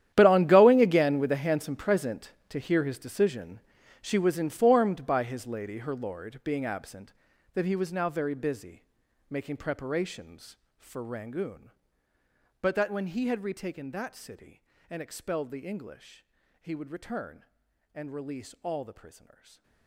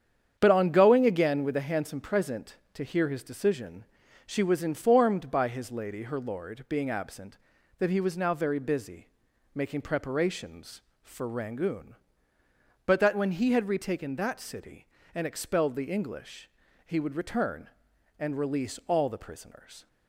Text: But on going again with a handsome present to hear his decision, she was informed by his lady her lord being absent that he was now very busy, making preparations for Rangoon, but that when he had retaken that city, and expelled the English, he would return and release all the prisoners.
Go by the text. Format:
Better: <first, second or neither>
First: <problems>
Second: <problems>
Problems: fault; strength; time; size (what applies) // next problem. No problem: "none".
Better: second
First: gets quieter; strong; throughout; 17.5 dB // starts louder than the rest; strong; until 1.1 s; 11 dB // stays silent after the last word; slight; from 19.3 s on; 0.5 s long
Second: starts louder than the rest; strong; until 1.4 s; 8.5 dB